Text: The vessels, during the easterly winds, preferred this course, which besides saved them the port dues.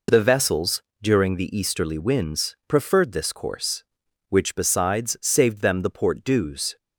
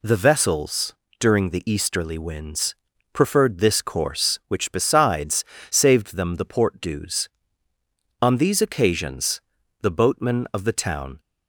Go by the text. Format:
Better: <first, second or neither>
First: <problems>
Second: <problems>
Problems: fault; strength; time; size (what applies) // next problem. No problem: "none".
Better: first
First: none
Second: pauses between "besides" and "saved"; slight; at 5.4 s; 0.24 s long // goes on to say "On these occasions the boatmen of the town"; strong; from 8.1 s on; 3.0 s long